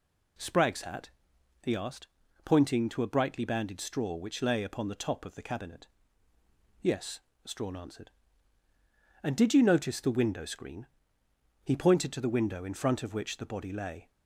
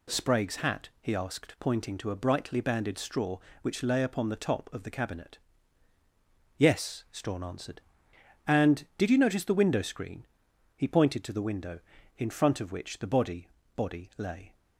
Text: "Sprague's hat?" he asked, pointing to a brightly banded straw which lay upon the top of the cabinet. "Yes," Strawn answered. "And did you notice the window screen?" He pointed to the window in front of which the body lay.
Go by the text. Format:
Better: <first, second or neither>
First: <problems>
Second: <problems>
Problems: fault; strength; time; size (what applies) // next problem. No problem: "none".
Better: first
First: none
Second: says "body" twice; at 13.7 s